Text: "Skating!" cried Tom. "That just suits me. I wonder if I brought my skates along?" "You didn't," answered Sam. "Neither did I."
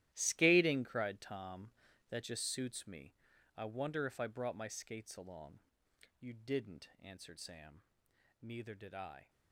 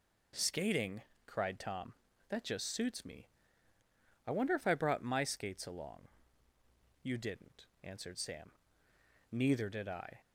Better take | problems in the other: second | gets quieter; strong; throughout; 15 dB

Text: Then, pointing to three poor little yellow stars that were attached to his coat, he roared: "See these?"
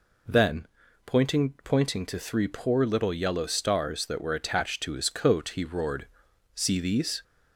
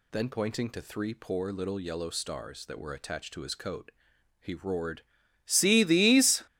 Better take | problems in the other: second | says "pointing" twice; at 1.6 s

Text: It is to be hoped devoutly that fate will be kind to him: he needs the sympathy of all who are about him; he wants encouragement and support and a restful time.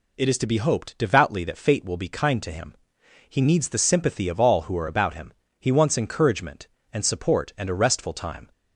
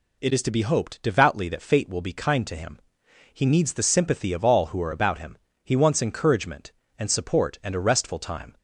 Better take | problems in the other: neither | none

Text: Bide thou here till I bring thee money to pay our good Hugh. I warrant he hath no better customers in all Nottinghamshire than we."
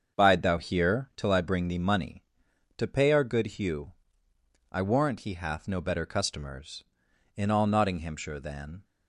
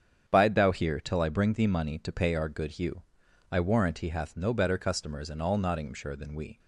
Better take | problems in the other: second | starts louder than the rest; until 1.2 s; 7 dB; strong in the second // stops before "we"; at 8.8 s

